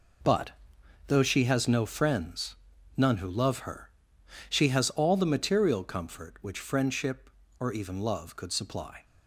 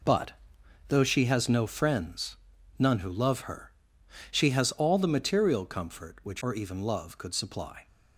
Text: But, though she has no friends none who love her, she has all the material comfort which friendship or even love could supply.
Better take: first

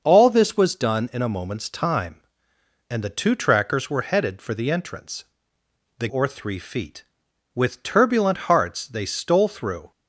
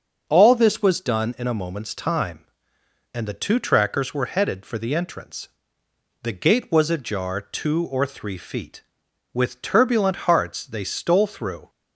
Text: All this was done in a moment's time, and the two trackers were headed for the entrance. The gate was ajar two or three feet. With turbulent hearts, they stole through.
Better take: second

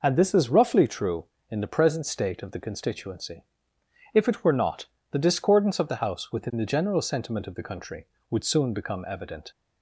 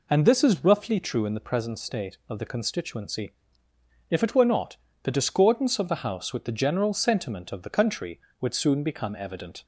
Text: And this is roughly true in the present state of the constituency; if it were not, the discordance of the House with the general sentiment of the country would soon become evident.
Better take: second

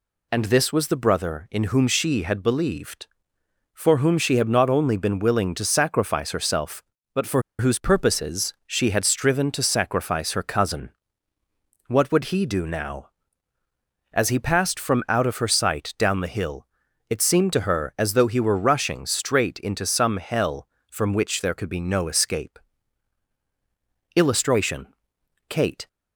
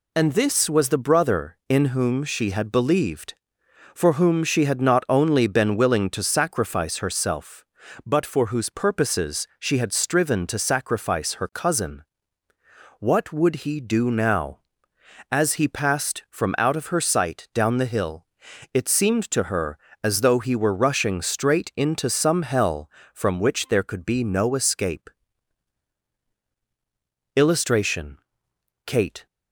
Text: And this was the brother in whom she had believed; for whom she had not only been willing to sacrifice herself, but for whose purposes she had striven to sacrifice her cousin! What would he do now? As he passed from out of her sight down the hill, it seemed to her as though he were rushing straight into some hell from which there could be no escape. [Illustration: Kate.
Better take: second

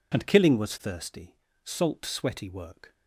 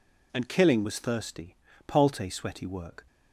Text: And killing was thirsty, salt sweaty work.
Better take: first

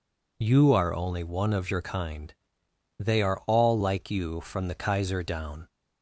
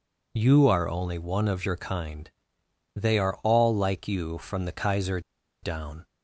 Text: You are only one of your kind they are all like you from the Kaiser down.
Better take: first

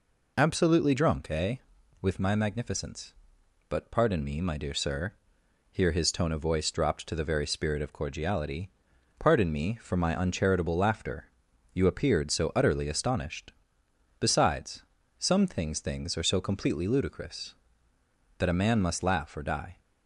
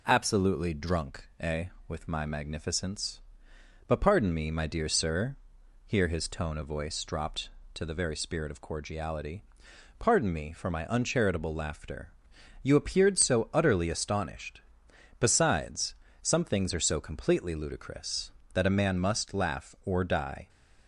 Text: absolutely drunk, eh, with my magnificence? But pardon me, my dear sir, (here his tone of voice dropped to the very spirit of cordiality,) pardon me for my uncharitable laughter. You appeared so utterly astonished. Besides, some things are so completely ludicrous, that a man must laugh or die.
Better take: second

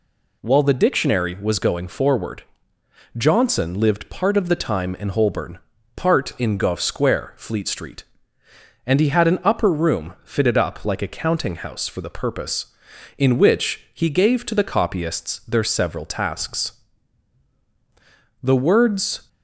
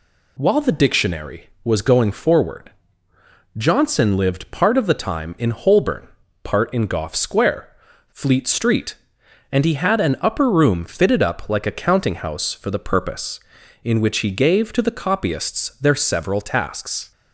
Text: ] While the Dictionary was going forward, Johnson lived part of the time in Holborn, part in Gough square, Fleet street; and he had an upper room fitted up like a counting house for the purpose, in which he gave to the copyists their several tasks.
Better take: second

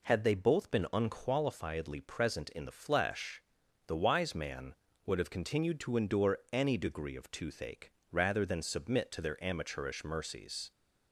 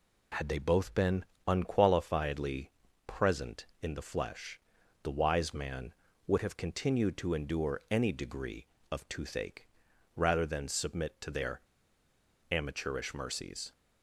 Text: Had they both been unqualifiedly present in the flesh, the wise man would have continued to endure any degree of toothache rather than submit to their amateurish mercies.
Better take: first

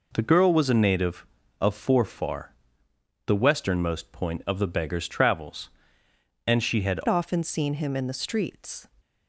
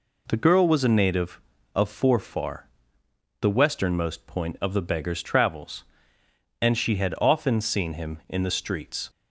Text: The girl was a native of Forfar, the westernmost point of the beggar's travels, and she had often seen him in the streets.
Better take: second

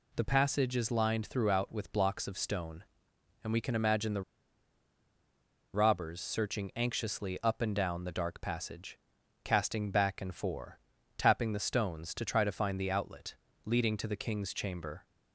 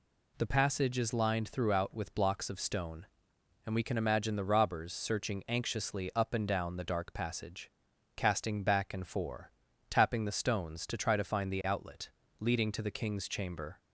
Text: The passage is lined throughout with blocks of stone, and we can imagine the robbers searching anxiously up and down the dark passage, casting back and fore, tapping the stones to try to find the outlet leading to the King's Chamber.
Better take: second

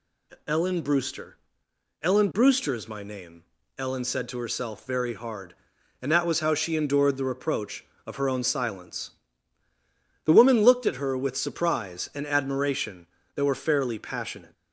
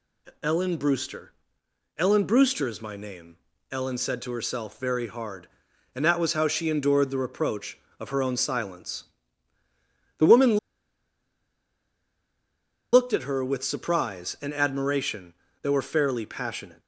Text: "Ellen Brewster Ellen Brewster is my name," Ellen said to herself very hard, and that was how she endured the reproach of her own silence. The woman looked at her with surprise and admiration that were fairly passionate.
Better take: first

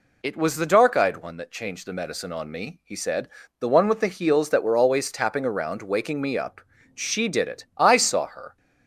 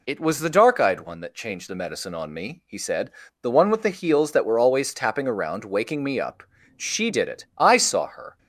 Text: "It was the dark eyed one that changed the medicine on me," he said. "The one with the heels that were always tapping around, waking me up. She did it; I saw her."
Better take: neither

